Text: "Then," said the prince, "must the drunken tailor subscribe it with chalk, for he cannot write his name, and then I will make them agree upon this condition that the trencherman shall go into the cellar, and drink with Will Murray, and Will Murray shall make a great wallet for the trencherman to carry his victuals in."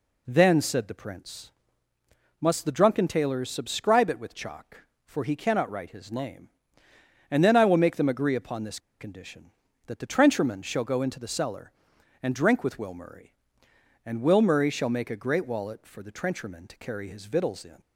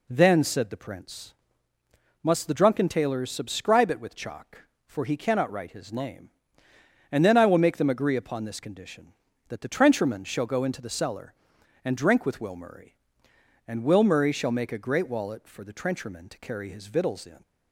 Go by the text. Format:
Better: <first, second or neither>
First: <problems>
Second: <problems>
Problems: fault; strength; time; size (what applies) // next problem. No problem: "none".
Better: second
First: pauses between "this" and "condition"; slight; at 8.7 s; 0.20 s long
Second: none